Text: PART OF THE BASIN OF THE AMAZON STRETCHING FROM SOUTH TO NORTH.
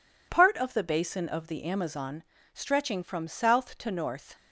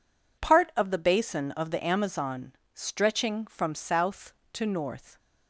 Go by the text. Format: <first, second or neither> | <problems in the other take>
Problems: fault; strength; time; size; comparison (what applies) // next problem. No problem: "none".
neither | pauses between "AMAZON" and "STRETCHING"; slight; the same in both